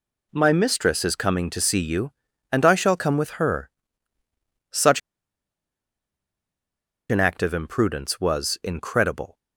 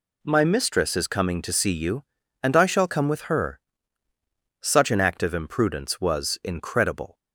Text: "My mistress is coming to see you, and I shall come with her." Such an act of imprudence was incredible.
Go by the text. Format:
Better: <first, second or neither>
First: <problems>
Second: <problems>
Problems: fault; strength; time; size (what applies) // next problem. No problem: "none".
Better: second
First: pauses between "Such" and "an"; strong; at 4.9 s; 2.1 s long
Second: none